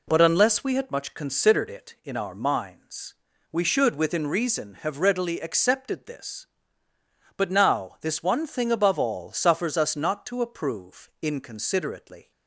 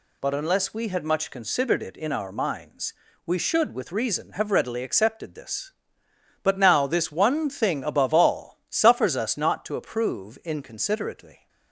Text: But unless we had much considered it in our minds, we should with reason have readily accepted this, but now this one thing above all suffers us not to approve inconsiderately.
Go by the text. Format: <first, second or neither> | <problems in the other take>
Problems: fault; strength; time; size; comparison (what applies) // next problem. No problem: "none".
second | says "within" for "with"; at 3.9 s